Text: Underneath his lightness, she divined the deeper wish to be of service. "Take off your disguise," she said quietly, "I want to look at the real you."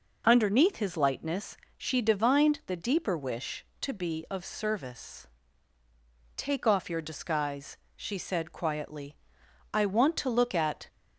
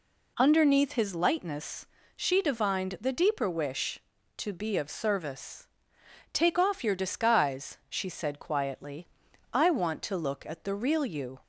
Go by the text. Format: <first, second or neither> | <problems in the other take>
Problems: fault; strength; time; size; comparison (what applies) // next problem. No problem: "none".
second | stops before "the real you"; at 10.8 s